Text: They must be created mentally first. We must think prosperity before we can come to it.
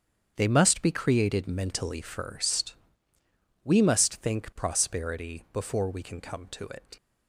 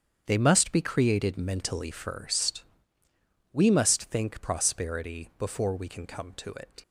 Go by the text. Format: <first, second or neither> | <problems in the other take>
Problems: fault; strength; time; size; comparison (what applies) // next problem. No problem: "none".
neither | starts louder than the rest; strong; the same in both